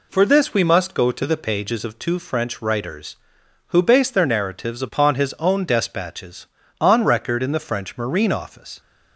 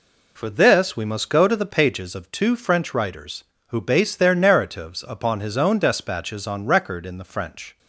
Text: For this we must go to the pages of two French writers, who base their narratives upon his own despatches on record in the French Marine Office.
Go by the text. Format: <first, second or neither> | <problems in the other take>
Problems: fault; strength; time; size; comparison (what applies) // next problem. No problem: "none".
first | stops before "Marine Office"; at 7.7 s